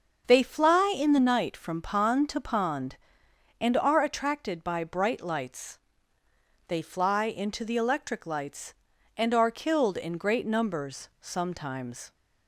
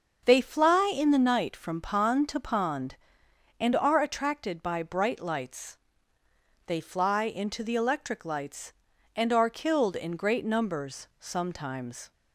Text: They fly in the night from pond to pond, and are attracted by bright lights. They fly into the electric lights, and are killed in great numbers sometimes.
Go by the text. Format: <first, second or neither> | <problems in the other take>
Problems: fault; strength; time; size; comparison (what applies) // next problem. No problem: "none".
neither | starts louder than the rest; the same in both